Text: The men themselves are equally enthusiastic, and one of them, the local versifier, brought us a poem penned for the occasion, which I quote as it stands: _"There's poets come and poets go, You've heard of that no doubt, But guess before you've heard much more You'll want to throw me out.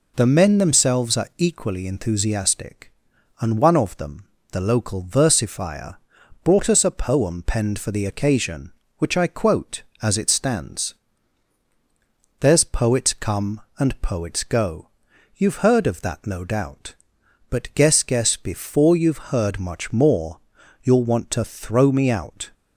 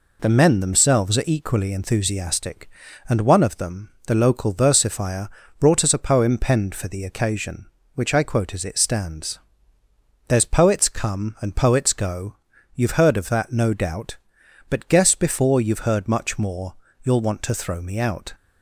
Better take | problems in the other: second | says "guess" twice; at 18.0 s // pauses between "more" and "You'll"; noticeable; at 20.3 s; 0.46 s long; slight in the second

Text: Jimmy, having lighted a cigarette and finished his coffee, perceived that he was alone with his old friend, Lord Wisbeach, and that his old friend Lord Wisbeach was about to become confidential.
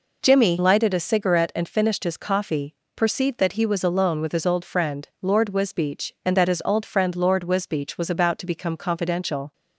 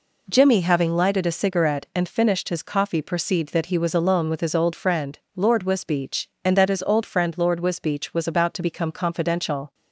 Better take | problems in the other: second | skips "having"; at 0.5 s

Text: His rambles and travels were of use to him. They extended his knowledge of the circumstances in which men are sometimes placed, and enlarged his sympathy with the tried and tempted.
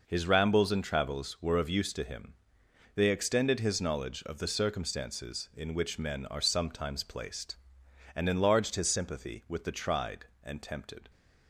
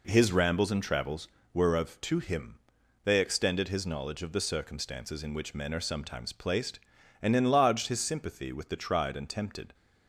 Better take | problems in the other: first | skips "use"; at 2.0 s

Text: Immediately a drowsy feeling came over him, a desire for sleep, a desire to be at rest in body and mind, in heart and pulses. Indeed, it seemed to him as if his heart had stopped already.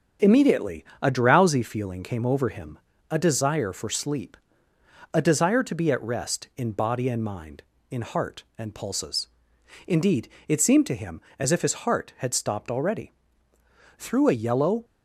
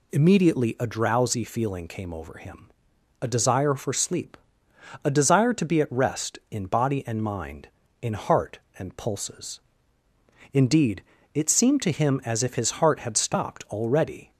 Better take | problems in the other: second | starts louder than the rest; until 1.3 s; 7 dB // pauses between "Immediately" and "a"; slight; at 0.8 s; 0.16 s long // goes on to say "Through a yellow"; noticeable; from 13.9 s on; 0.88 s long

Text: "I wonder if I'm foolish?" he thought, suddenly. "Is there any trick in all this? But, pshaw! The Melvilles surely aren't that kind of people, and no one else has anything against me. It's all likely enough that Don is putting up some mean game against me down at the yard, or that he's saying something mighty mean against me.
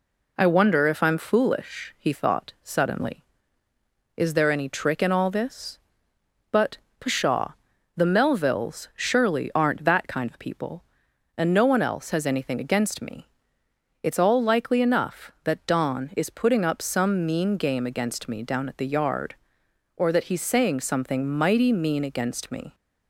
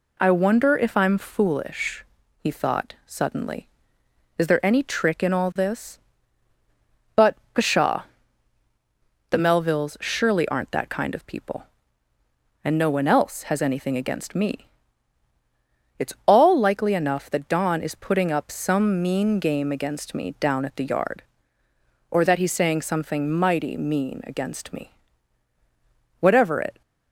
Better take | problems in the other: first | goes on to say "Whatever it"; noticeable; from 26.1 s on; 0.62 s long

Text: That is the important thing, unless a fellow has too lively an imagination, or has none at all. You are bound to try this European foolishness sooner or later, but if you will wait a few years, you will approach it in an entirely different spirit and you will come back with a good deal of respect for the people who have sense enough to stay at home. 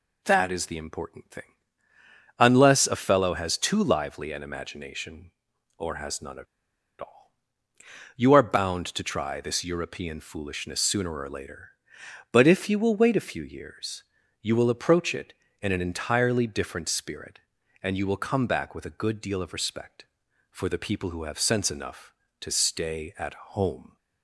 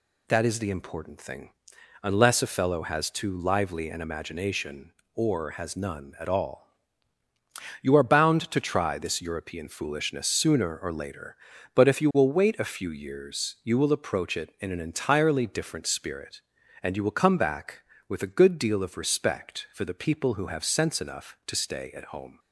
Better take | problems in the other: second | pauses between "at" and "all"; noticeable; at 6.4 s; 0.56 s long

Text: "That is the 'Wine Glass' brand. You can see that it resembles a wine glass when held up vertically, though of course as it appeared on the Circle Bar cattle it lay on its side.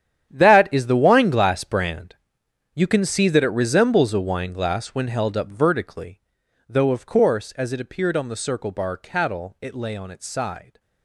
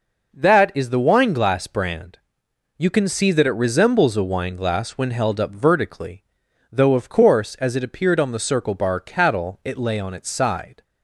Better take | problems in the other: second | gets quieter; strong; throughout; 14.5 dB

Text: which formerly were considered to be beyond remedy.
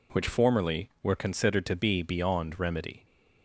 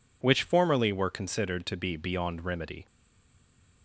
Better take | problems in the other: first | stays silent after the last word; from 2.8 s on; 1.0 s long

